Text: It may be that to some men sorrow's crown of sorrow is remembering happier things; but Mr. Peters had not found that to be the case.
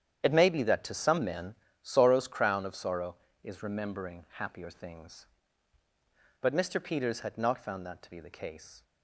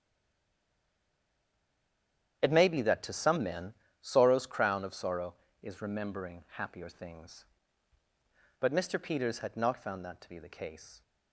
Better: first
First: starts louder than the rest; strong; until 1.2 s; 9 dB // pauses between "men" and "sorrow's"; slight; at 1.5 s; 0.26 s long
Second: stays silent before the first word; until 2.4 s; 2.4 s long // starts louder than the rest; strong; until 3.4 s; 9 dB // pauses between "men" and "sorrow's"; slight; at 3.7 s; 0.26 s long

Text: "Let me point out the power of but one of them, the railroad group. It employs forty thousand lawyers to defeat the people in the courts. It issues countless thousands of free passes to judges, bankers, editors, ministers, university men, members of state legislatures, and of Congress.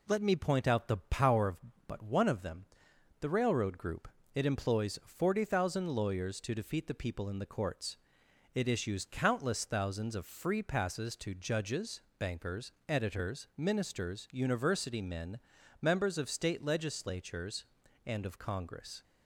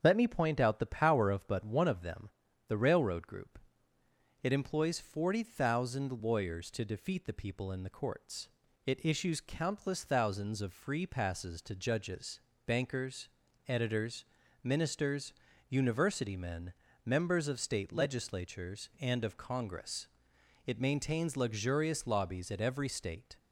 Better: first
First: none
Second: starts louder than the rest; strong; until 1.0 s; 7 dB // goes on to say "It maintains luxurious lobbies at every state"; strong; from 20.6 s on; 2.7 s long

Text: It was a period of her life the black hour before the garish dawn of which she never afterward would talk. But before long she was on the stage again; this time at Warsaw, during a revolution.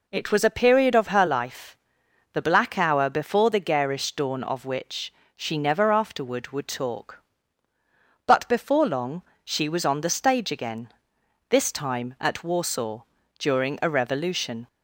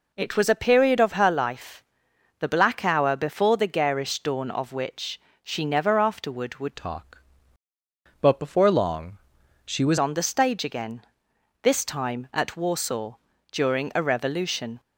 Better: first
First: pauses between "life" and "the"; noticeable; at 1.7 s; 0.56 s long // pauses between "which" and "she"; slight; at 5.1 s; 0.26 s long // pauses between "long" and "she"; slight; at 9.2 s; 0.20 s long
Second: pauses between "life" and "the"; noticeable; at 1.8 s; 0.56 s long // pauses between "which" and "she"; slight; at 5.1 s; 0.26 s long // changes voice from "talk" to "was"; from 6.7 to 9.9 s; 3.2 s long // pauses between "long" and "she"; noticeable; at 9.1 s; 0.48 s long

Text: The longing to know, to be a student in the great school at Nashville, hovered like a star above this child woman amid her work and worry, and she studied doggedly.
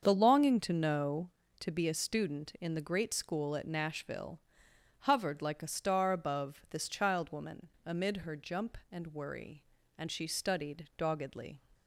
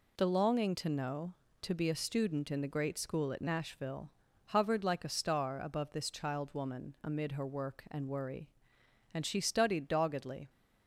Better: second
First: starts louder than the rest; until 1.0 s; 7 dB // pauses between "woman" and "amid"; slight; at 7.6 s; 0.16 s long // says "jump" for "work"; at 8.3 s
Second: none

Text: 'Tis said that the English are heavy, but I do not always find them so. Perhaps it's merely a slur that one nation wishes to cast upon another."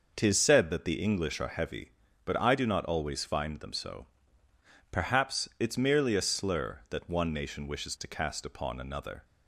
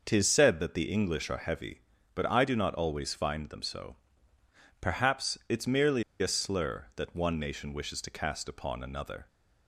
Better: first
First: none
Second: pauses between "merely" and "a"; slight; at 6.0 s; 0.17 s long

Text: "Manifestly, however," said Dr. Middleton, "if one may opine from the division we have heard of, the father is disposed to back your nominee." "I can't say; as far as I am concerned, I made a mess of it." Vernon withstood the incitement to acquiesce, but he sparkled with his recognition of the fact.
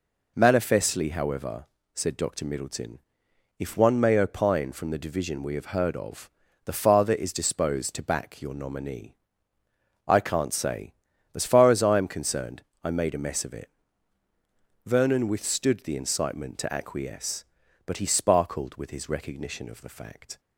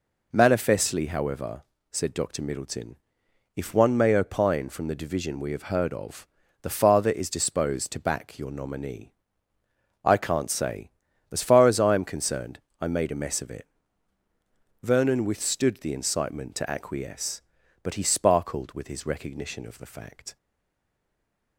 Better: first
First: none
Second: stays silent after the last word; noticeable; from 20.3 s on; 1.2 s long

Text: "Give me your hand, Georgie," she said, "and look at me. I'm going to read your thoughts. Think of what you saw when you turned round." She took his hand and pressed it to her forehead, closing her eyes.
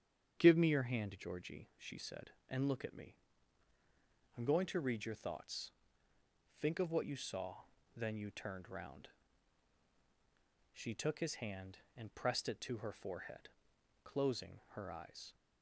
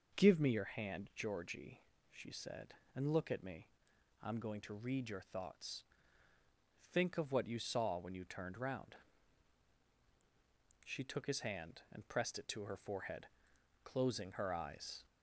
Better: second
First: starts louder than the rest; strong; until 1.4 s; 8 dB // says "then" for "when"; at 7.9 s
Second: none

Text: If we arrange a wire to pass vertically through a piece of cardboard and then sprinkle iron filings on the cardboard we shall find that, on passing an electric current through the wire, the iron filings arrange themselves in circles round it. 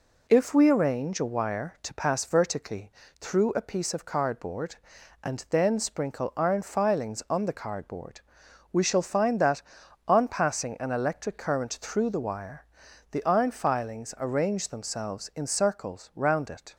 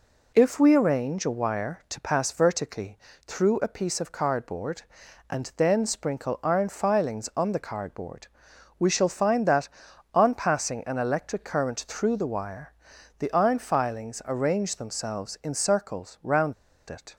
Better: first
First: pauses between "vertically" and "through"; slight; at 2.8 s; 0.30 s long // pauses between "cardboard" and "we"; noticeable; at 8.2 s; 0.50 s long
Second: pauses between "vertically" and "through"; slight; at 2.9 s; 0.30 s long // pauses between "cardboard" and "we"; noticeable; at 8.2 s; 0.50 s long // pauses between "round" and "it"; slight; at 16.5 s; 0.35 s long

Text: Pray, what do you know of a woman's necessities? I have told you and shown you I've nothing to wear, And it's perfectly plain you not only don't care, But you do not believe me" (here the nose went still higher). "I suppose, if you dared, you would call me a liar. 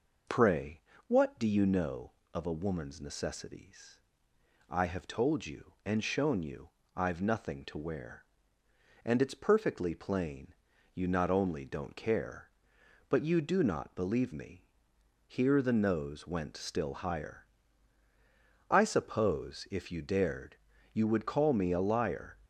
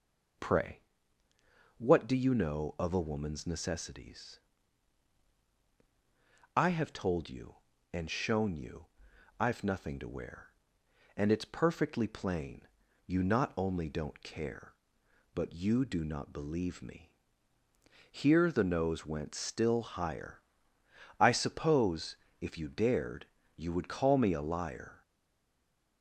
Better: first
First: pauses between "you" and "I've"; slight; at 6.6 s; 0.26 s long // pauses between "plain" and "you"; at 10.5 s; 0.40 s long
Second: pauses between "you" and "I've"; noticeable; at 8.8 s; 0.54 s long // pauses between "plain" and "you"; at 12.6 s; 0.40 s long // stays silent after the last word; from 25.0 s on; 1.0 s long

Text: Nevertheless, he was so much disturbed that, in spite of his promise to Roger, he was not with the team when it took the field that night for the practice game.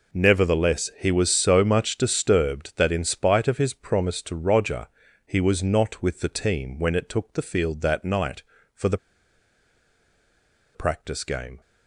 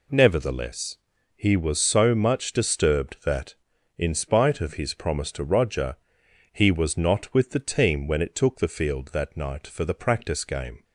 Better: second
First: pauses between "the" and "practice"; strong; at 8.9 s; 1.7 s long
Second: none

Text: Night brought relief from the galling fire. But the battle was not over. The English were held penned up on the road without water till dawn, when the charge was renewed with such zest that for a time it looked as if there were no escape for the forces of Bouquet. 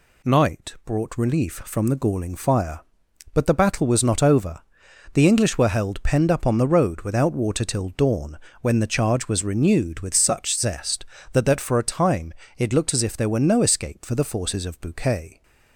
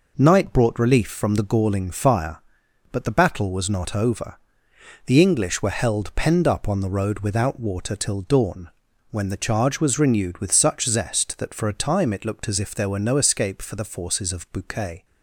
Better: second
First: says "that" twice; at 11.4 s // pauses between "time" and "it"; slight; at 12.3 s; 0.24 s long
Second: none

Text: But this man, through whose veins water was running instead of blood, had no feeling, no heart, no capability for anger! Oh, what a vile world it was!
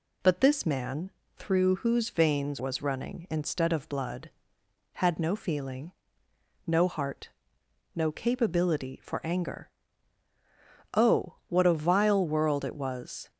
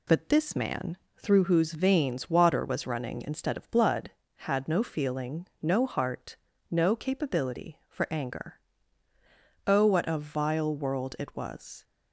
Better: second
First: skips "water"; at 2.5 s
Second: none

